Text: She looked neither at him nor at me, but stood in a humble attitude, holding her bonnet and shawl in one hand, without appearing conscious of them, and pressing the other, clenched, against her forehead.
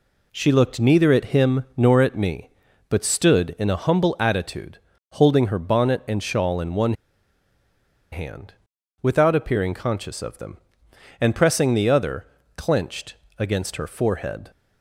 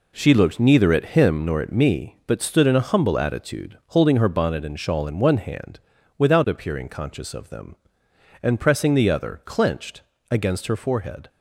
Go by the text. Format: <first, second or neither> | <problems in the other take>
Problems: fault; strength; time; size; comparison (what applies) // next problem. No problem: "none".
second | pauses between "one" and "hand"; at 6.9 s; 1.1 s long